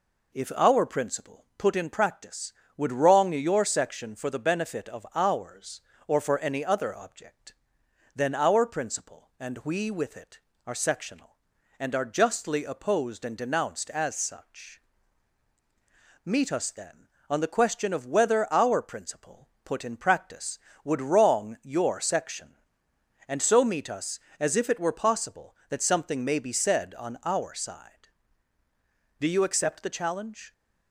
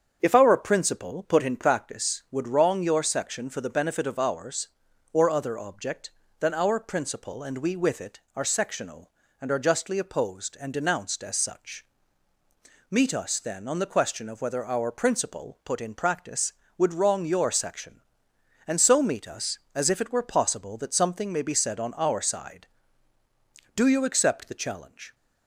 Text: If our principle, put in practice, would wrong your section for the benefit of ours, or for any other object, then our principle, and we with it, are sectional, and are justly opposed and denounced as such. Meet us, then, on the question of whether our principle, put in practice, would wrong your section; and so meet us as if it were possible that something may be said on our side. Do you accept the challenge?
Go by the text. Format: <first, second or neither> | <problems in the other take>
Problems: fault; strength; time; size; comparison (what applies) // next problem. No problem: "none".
first | starts louder than the rest; strong; until 1.2 s; 7.5 dB // skips "for any"; at 5.3 s